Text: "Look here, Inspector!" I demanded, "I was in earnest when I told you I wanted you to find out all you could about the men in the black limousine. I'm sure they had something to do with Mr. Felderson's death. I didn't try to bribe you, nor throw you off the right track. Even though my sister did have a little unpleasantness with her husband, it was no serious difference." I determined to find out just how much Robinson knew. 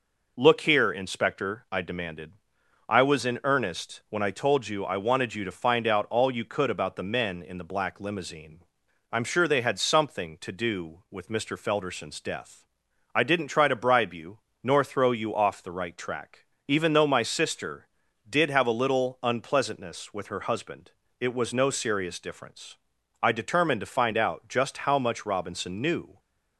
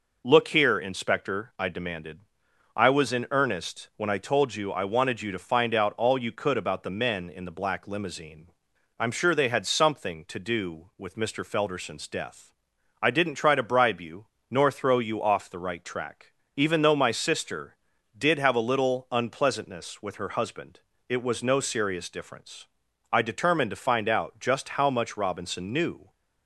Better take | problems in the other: neither | none

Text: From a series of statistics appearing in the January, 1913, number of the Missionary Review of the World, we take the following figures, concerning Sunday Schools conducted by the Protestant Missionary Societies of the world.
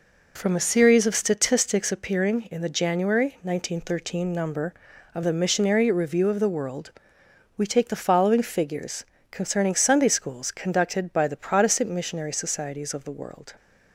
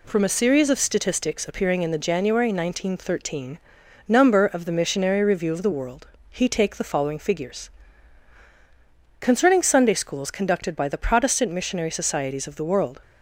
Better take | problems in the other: first | says "he" for "we"; at 6.2 s

